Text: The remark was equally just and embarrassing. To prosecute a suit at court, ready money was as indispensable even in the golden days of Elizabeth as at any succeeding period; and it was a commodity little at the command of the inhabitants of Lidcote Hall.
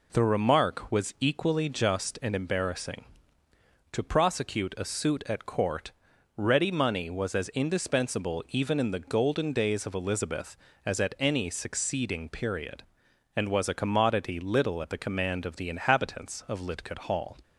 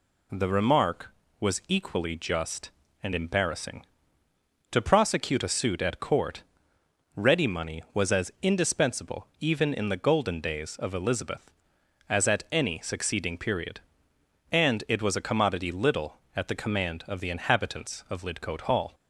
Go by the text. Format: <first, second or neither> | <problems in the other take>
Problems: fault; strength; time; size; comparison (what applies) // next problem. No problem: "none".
second | skips "it"; at 13.4 s